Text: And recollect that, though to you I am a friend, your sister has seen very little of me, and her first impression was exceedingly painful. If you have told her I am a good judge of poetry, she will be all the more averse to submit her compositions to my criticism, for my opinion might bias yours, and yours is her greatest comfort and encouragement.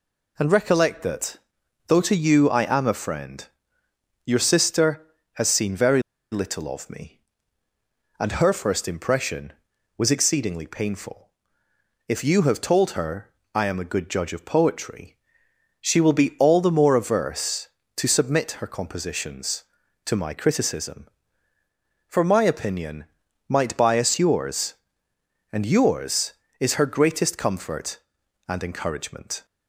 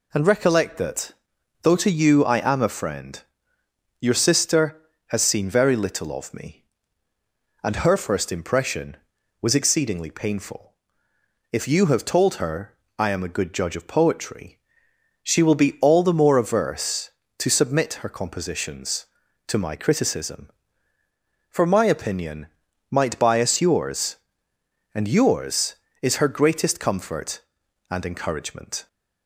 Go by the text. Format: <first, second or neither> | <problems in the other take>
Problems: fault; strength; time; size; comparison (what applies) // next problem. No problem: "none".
second | pauses between "very" and "little"; slight; at 6.0 s; 0.30 s long // pauses between "her" and "I"; slight; at 13.2 s; 0.24 s long; slight in the second // pauses between "opinion" and "might"; at 23.0 s; 0.42 s long; also in the second